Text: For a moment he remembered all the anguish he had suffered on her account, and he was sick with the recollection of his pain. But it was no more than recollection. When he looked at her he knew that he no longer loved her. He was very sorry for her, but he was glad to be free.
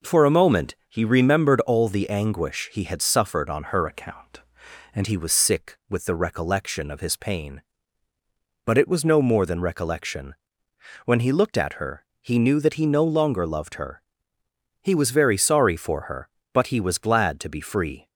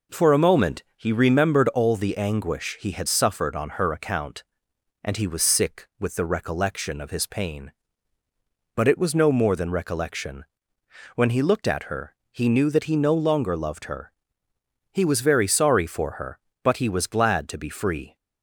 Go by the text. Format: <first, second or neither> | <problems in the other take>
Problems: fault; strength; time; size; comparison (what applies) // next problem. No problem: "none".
second | changes voice from "account" to "and"; from 3.8 to 5.0 s; 1.2 s long // pauses between "her" and "he"; slight; at 12.0 s; 0.18 s long; slight in the second